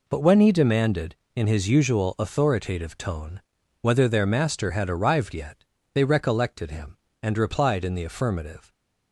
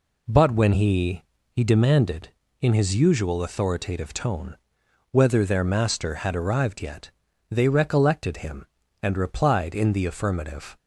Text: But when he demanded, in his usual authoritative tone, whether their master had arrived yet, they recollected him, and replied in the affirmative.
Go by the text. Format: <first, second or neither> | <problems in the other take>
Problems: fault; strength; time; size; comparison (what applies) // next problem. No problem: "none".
first | says "he" twice; at 1.4 s